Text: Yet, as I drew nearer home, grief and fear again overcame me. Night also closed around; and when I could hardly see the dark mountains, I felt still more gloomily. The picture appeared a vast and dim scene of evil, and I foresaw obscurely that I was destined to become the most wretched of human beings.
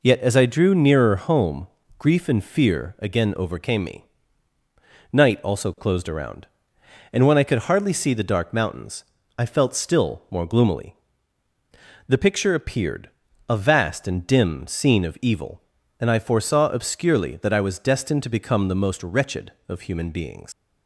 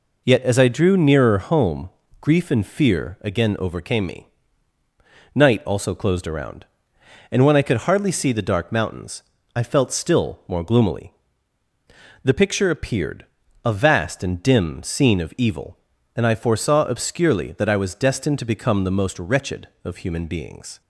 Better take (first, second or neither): second